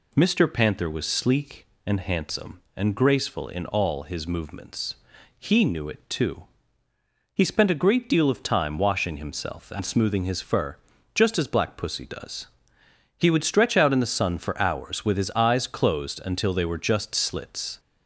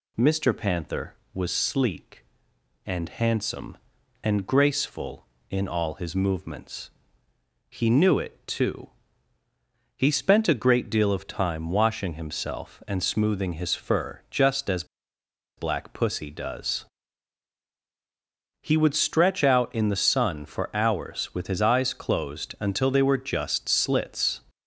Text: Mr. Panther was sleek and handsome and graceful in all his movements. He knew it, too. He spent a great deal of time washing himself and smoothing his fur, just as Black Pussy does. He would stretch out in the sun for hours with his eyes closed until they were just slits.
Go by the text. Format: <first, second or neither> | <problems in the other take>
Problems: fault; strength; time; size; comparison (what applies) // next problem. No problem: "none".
first | pauses between "as" and "Black"; noticeable; at 14.8 s; 0.73 s long